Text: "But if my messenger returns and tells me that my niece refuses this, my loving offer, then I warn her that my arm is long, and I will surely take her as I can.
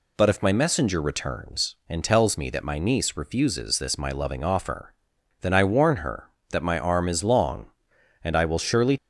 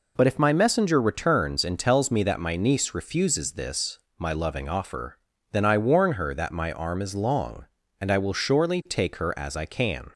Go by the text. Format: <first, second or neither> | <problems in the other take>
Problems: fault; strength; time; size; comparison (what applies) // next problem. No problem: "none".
second | stops before "take her as I can"; at 8.9 s